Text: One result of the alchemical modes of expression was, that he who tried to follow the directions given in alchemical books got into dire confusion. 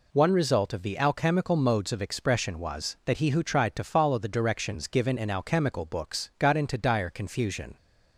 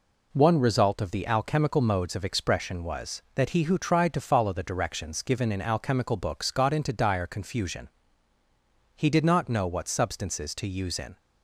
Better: first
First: none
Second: goes on to say "He did not know what substances to use in"; strong; from 8.9 s on; 2.2 s long

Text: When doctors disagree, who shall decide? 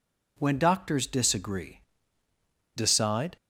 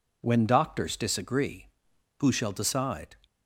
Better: second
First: skips "who shall"; at 2.2 s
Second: none

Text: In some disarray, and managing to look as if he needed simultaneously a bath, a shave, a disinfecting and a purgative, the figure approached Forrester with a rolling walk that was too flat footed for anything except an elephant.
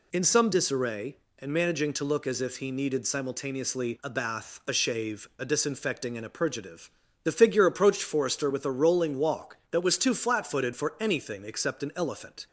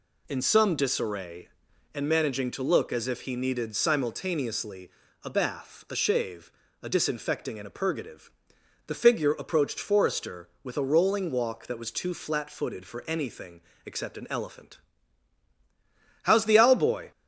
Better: first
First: none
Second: pauses between "simultaneously" and "a"; slight; at 4.8 s; 0.34 s long // pauses between "anything" and "except"; slight; at 13.6 s; 0.26 s long // goes on to say "How's the Owl boy"; noticeable; from 16.2 s on; 0.88 s long

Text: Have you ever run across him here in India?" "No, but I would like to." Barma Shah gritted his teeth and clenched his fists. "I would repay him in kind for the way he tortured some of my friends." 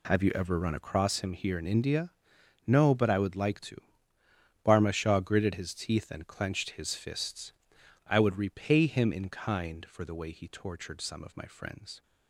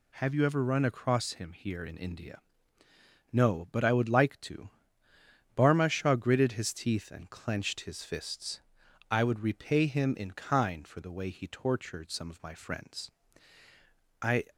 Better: first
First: none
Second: goes on to say "I"; slight; from 14.2 s on; 0.26 s long

